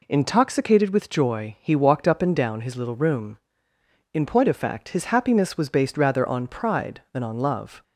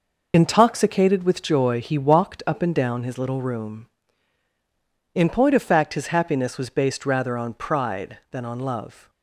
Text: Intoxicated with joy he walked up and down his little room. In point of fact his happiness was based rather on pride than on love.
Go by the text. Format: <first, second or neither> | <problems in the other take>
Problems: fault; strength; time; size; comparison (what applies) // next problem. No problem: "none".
first | loses the start of "Intoxicated"; at 0.3 s; 60 ms